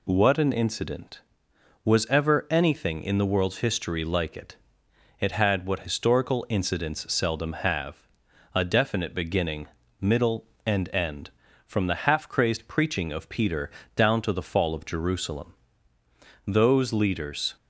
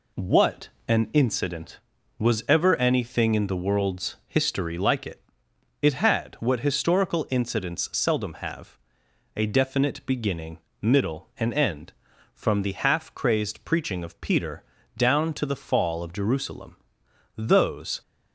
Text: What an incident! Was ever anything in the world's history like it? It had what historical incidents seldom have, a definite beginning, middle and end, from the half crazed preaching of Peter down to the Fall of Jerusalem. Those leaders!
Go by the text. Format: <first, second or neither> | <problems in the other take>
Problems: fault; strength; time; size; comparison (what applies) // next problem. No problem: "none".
first | pauses between "What" and "an"; slight; at 0.6 s; 0.18 s long // pauses between "Peter" and "down"; slight; at 14.6 s; 0.34 s long; slight in the first // stops before "leaders"; at 18.0 s